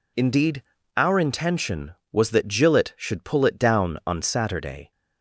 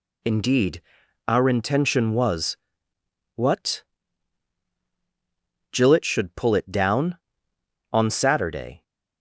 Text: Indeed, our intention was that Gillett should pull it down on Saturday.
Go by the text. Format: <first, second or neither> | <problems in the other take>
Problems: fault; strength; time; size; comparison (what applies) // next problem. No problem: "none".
first | says "what" for "that"; at 3.3 s